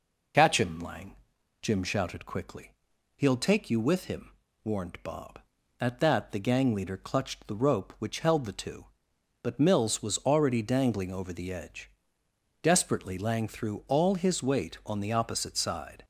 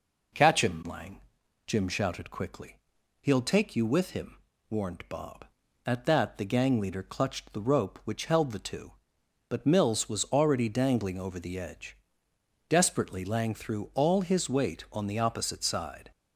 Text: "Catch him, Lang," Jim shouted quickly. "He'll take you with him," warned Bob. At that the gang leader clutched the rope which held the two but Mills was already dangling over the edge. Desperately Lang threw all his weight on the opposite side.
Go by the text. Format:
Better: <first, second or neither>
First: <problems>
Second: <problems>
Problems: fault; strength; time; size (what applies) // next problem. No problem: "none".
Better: second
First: loses the start of "Catch"; at 0.3 s; 50 ms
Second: none